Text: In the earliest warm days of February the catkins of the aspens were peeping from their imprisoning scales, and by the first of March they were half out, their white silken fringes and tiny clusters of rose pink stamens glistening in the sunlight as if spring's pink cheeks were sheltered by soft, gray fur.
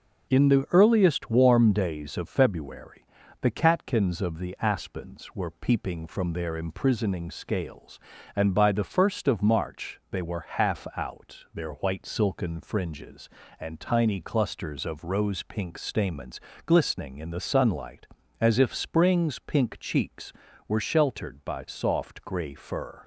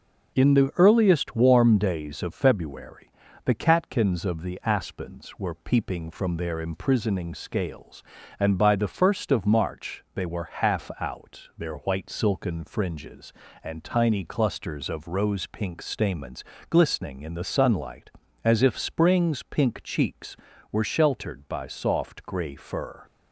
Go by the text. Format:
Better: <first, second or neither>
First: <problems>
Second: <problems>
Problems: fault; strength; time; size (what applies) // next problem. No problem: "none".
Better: neither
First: pauses between "February" and "the"; slight; at 3.0 s; 0.34 s long // pauses between "stamens" and "glistening"; slight; at 16.4 s; 0.24 s long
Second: pauses between "February" and "the"; slight; at 3.1 s; 0.32 s long // pauses between "stamens" and "glistening"; slight; at 16.4 s; 0.24 s long